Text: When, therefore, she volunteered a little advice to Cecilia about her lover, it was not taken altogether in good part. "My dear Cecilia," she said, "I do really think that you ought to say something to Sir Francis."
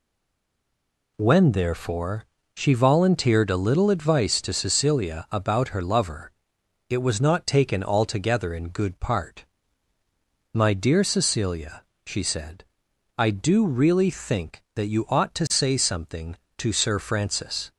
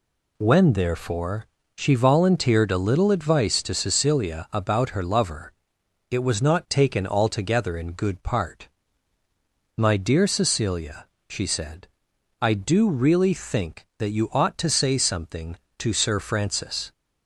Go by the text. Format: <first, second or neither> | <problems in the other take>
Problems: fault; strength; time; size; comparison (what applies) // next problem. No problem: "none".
second | stays silent before the first word; noticeable; until 1.1 s; 1.1 s long